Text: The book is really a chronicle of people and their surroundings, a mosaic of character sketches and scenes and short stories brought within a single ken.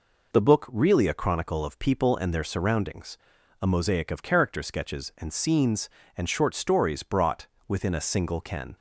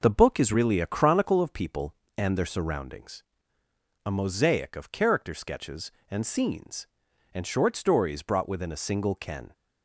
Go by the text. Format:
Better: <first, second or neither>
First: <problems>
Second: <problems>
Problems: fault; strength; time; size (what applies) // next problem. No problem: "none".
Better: second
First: skips "is"; at 0.6 s // pauses between "brought" and "within"; slight; at 7.4 s; 0.20 s long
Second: none